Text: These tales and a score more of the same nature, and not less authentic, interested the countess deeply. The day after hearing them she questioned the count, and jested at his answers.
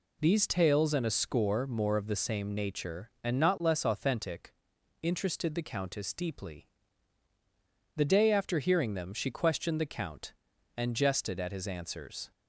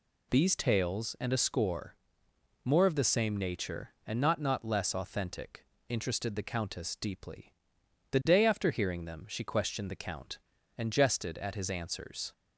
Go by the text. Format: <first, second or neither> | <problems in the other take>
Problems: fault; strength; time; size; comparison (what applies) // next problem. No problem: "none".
first | pauses between "score" and "more"; noticeable; at 1.9 s; 0.68 s long // says "not" twice; at 4.3 s